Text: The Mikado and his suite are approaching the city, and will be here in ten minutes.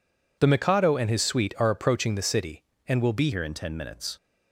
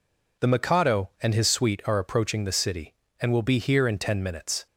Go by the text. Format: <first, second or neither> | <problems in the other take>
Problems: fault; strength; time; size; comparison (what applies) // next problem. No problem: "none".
second | changes voice at "here"; from 3.3 s on; 0.8 s long